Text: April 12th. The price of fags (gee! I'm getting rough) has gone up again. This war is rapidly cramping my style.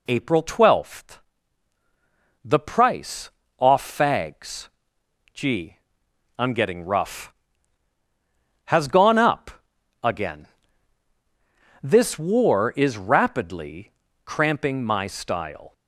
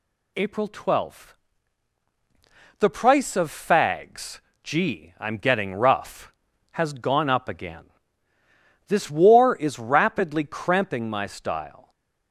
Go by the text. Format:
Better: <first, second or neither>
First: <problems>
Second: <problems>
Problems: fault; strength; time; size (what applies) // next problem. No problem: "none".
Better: second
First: says "off" for "of"; at 3.5 s // pauses between "up" and "again"; noticeable; at 9.5 s; 0.54 s long // pauses between "rapidly" and "cramping"; slight; at 13.9 s; 0.34 s long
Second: none